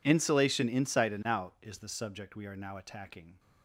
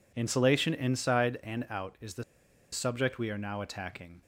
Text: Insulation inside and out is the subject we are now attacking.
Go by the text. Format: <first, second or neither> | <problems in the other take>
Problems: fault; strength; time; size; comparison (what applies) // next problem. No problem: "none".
first | pauses between "the" and "subject"; noticeable; at 2.2 s; 0.49 s long